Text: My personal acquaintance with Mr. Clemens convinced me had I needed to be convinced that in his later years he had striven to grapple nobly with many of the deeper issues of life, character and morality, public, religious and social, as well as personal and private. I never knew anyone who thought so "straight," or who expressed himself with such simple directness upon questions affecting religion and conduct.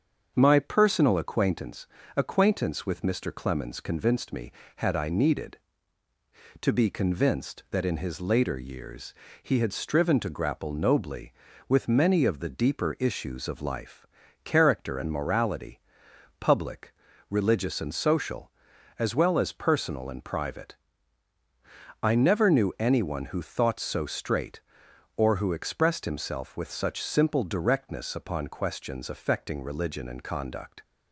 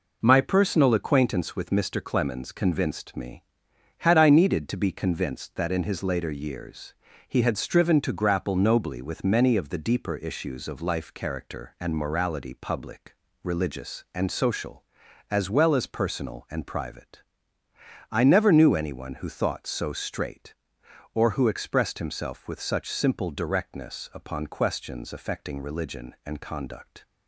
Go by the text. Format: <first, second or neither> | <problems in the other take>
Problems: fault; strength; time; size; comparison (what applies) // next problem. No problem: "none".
second | starts louder than the rest; until 1.3 s; 7 dB // says "acquaintance" twice; at 2.1 s // pauses between "years" and "he"; slight; at 9.1 s; 0.30 s long; slight in the second